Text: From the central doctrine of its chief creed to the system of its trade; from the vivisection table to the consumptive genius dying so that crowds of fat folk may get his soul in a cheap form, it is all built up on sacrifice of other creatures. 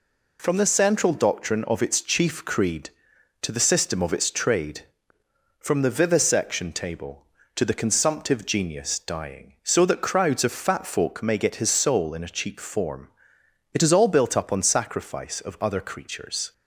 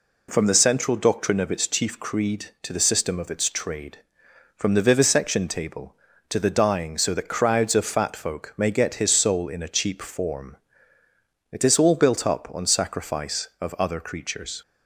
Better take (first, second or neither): first